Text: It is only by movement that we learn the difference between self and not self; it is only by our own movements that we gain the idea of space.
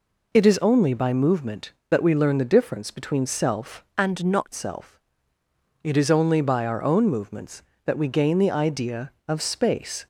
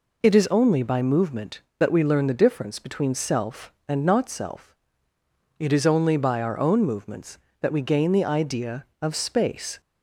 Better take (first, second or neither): second